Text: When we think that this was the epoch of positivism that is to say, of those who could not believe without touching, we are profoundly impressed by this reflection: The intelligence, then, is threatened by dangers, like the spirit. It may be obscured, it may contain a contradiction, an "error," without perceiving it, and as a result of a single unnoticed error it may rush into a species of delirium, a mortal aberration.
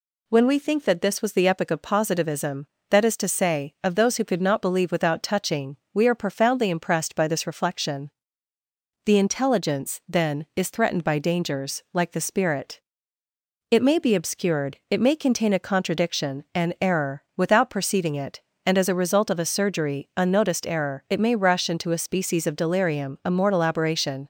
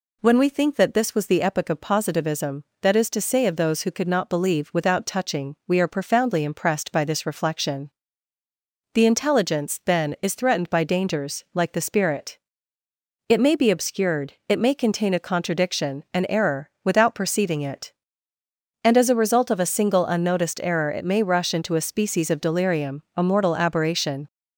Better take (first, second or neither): second